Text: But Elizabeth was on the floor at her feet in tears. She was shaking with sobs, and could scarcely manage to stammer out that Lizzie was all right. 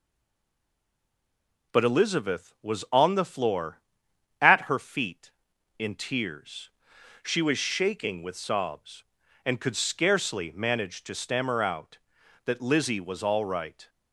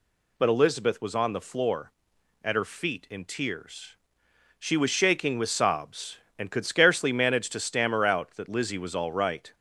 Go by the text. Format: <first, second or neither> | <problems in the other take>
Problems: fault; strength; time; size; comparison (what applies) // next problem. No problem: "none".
second | stays silent before the first word; noticeable; until 1.7 s; 1.7 s long